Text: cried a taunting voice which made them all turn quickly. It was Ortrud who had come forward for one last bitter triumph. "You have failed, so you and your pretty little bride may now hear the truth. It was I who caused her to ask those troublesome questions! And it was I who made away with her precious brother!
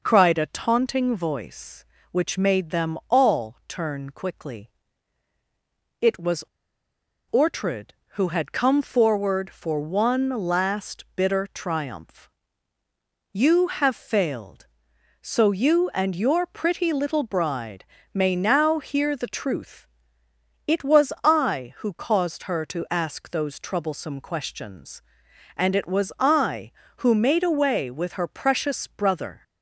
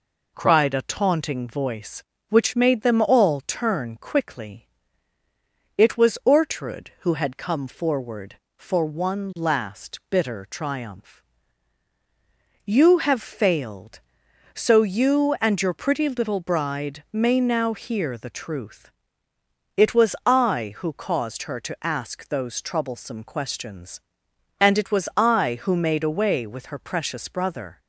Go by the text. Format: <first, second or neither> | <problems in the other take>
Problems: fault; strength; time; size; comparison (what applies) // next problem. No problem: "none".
second | pauses between "was" and "Ortrud"; noticeable; at 6.4 s; 0.90 s long // pauses between "bride" and "may"; slight; at 17.8 s; 0.28 s long